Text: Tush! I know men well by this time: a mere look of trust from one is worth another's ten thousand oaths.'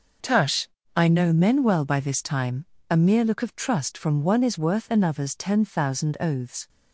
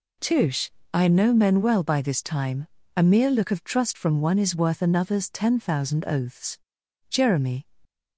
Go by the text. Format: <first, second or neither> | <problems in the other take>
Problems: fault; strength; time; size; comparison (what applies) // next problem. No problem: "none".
first | goes on to say "Jeremy"; from 7.1 s on; 0.56 s long